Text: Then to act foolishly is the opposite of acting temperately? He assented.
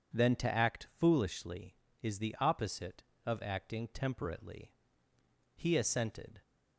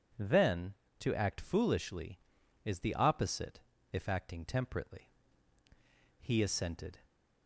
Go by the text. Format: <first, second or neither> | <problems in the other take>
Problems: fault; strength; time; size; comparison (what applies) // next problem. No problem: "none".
first | says "if" for "of"; at 3.9 s